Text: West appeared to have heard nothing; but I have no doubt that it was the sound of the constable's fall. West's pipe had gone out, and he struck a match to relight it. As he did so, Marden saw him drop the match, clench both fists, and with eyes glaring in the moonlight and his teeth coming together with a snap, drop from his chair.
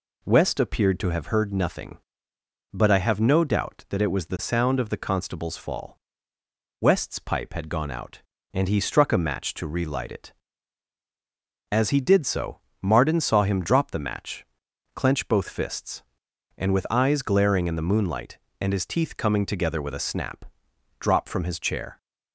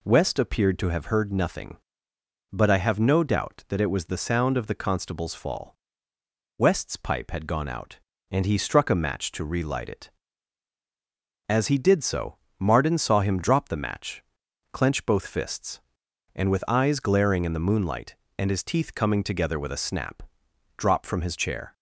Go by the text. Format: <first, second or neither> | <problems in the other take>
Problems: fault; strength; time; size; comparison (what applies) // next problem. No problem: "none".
neither | none